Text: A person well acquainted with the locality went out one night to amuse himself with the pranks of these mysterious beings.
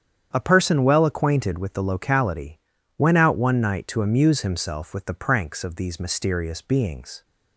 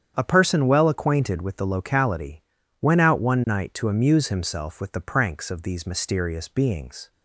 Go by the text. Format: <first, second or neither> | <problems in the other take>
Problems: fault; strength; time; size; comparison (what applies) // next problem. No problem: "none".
neither | starts louder than the rest; strong; the same in both // pauses between "locality" and "went"; the same in both